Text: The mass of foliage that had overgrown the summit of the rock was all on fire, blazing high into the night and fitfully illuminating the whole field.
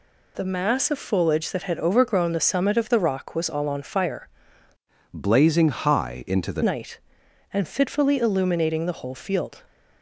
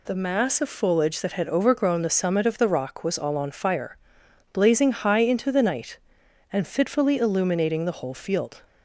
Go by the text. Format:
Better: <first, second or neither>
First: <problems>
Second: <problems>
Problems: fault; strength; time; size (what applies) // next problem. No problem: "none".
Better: second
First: changes voice from "blazing" to "the"; from 5.1 to 6.6 s; 1.5 s long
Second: none